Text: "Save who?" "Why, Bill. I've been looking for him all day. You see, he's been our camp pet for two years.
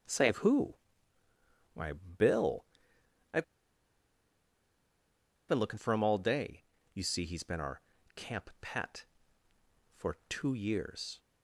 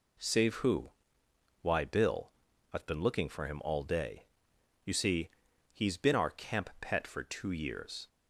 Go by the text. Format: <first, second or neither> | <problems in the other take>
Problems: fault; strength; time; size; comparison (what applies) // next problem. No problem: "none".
second | starts louder than the rest; until 2.0 s; 6.5 dB // pauses between "I've" and "been"; strong; at 3.4 s; 2.0 s long // pauses between "our" and "camp"; slight; at 7.8 s; 0.34 s long